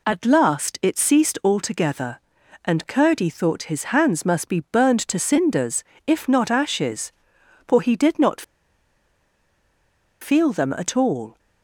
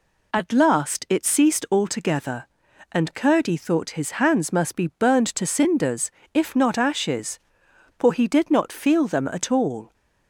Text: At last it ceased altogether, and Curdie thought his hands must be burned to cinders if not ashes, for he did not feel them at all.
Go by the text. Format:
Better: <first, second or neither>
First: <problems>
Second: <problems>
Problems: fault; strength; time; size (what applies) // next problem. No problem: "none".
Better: second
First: pauses between "cinders" and "if"; slight; at 5.8 s; 0.24 s long // pauses between "not" and "feel"; strong; at 8.4 s; 1.7 s long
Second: pauses between "cinders" and "if"; slight; at 6.0 s; 0.24 s long